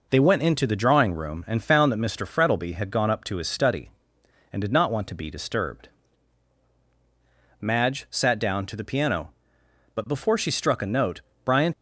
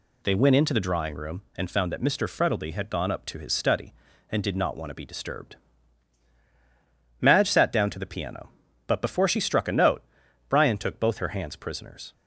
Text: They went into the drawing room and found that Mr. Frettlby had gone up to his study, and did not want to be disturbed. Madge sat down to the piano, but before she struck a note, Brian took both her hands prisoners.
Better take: second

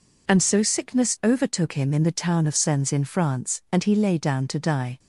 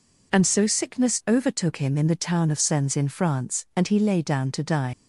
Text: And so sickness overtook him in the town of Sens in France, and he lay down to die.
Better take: first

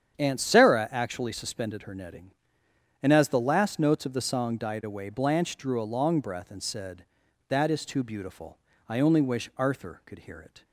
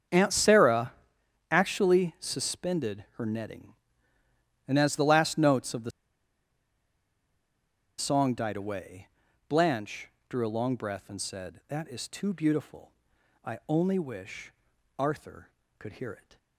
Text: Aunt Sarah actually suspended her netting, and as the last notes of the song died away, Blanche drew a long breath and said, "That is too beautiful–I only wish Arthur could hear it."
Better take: first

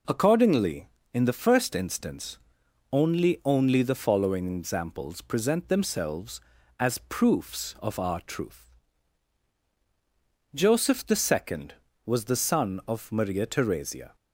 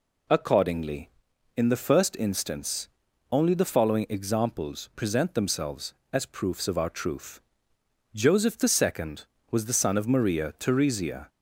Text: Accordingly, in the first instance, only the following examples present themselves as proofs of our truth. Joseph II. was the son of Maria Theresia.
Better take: second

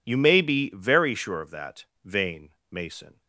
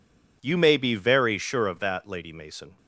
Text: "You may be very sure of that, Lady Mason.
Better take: second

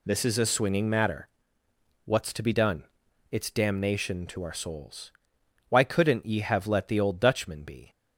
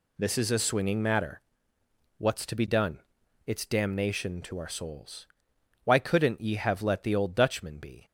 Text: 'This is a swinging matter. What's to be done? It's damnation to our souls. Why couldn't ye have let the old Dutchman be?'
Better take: neither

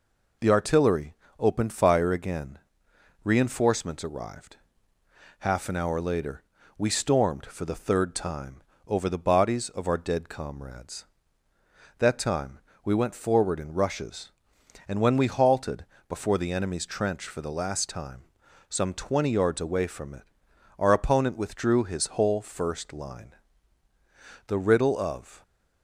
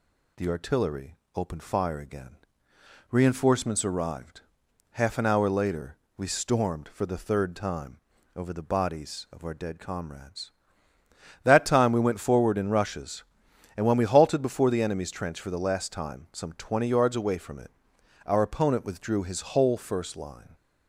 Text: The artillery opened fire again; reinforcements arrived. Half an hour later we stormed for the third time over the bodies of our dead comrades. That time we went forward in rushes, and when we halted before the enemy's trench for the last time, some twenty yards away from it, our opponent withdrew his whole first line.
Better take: second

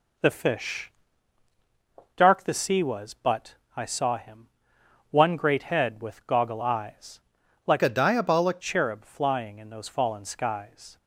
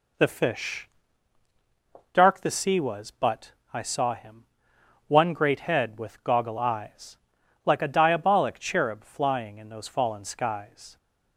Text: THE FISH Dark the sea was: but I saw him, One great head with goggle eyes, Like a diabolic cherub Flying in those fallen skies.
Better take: second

